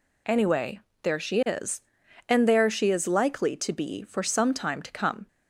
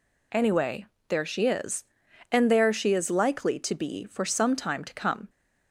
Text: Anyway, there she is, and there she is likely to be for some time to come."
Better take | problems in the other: neither | none

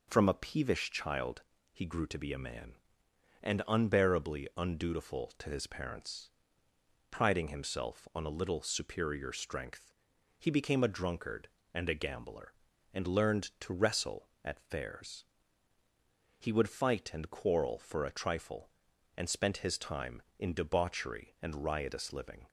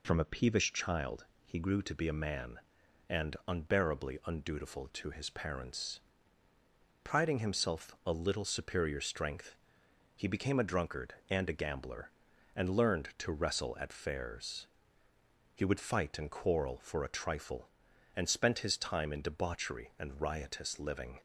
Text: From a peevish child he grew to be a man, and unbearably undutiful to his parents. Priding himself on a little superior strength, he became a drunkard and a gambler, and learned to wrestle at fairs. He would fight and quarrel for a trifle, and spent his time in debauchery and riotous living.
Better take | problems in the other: first | pauses between "child" and "he"; slight; at 1.2 s; 0.20 s long; slight in the first // skips "on"; at 8.0 s

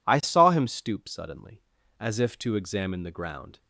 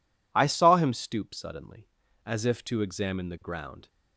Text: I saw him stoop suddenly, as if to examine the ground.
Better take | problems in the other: neither | none

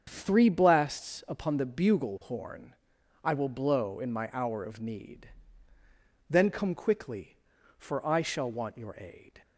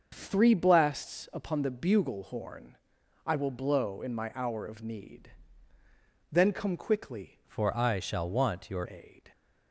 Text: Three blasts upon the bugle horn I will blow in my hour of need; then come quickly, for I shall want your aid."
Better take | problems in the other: first | starts louder than the rest; until 1.1 s; 6 dB; also in the first // pauses between "horn" and "I"; noticeable; at 2.7 s; 0.48 s long; noticeable in the first // changes voice from "for" to "your"; from 7.4 to 8.8 s; 1.4 s long

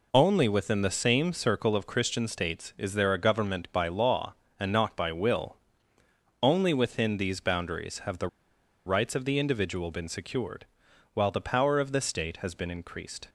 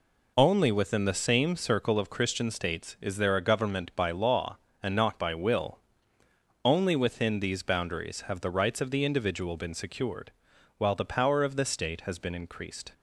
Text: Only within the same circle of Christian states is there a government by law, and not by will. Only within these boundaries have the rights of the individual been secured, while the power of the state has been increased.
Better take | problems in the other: second | pauses between "the" and "rights"; noticeable; at 8.2 s; 0.59 s long

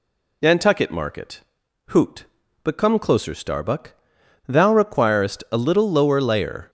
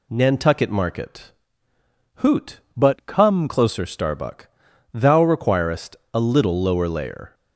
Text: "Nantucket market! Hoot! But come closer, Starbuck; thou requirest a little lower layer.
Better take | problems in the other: first | changes voice from "But" to "come"; from 2.7 to 3.4 s; 0.7 s long // pauses between "requirest" and "a"; slight; at 5.9 s; 0.16 s long

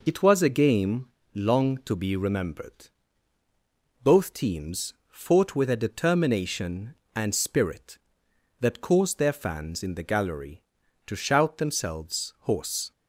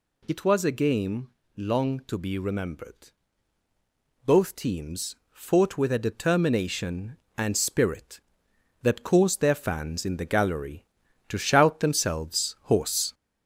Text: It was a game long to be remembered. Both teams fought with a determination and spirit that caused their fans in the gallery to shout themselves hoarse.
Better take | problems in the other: first | gets louder; throughout; 3.5 dB // pauses between "game" and "long"; slight; at 1.2 s; 0.30 s long; slight in the first

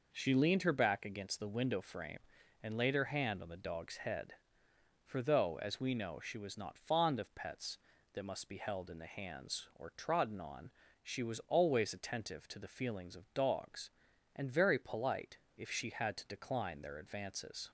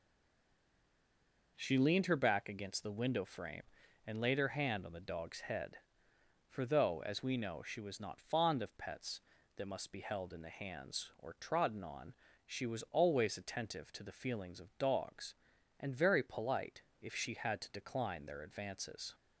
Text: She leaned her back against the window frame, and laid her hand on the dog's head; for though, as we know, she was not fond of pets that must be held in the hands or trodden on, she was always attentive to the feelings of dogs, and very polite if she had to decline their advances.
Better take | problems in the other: first | stays silent before the first word; noticeable; until 1.5 s; 1.5 s long // pauses between "polite" and "if"; slight; at 16.8 s; 0.18 s long; slight in the first

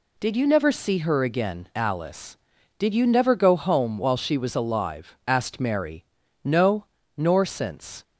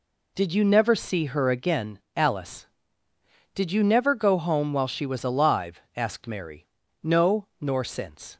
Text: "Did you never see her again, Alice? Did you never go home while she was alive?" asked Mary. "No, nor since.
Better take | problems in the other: neither | none

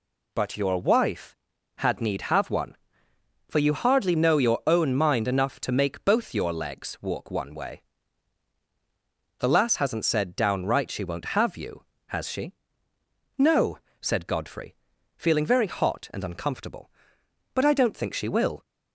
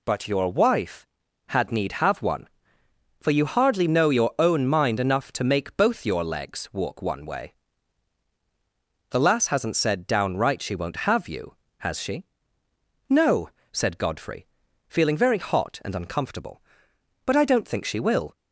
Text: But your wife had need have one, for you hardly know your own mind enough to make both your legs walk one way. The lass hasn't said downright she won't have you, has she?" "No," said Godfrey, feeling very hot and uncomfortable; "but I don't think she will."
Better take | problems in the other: neither | none

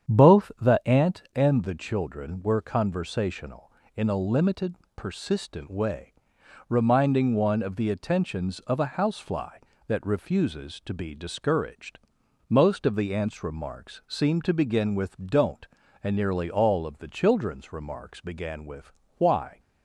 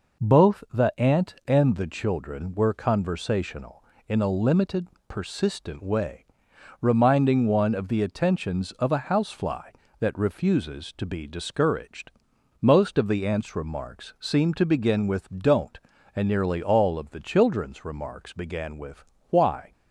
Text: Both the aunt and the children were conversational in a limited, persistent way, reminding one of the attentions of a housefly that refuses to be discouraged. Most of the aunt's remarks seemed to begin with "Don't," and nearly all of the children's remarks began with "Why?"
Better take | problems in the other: second | starts louder than the rest; strong; until 1.1 s; 8.5 dB // pauses between "with" and "Why"; slight; at 18.9 s; 0.24 s long; slight in the second

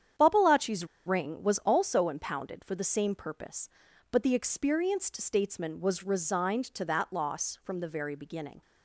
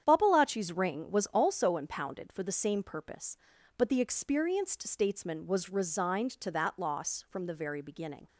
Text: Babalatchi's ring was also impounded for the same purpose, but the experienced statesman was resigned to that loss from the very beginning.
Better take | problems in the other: second | starts louder than the rest; strong; until 1.4 s; 9 dB; strong in the second // pauses between "Babalatchi's" and "ring"; slight; at 0.8 s; 0.21 s long

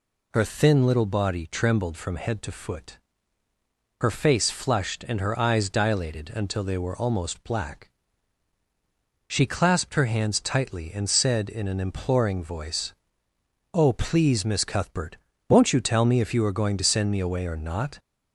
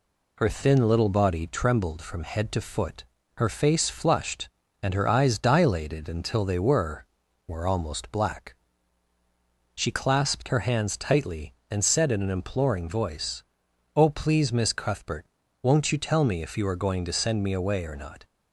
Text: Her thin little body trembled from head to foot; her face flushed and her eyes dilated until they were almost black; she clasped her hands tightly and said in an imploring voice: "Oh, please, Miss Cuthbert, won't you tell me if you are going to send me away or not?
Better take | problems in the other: first | says "were" twice; at 7.4 s

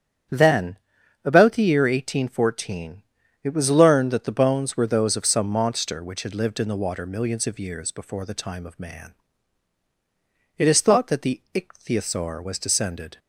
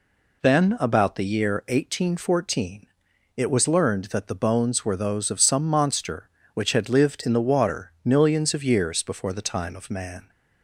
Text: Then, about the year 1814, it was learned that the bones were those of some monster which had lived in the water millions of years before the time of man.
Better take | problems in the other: second | starts louder than the rest; strong; until 1.7 s; 9.5 dB // goes on to say "It is thought that the Ichthyosaur was descended"; strong; from 10.5 s on; 2.6 s long

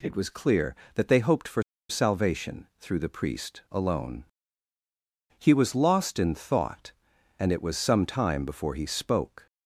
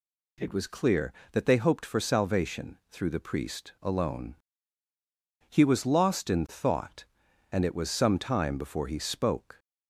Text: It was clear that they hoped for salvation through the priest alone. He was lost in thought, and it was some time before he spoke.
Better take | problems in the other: second | pauses between "for" and "salvation"; slight; at 1.6 s; 0.28 s long

